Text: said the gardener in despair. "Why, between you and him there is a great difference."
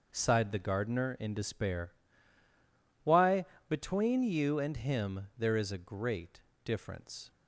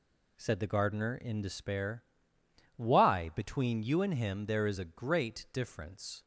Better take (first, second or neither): second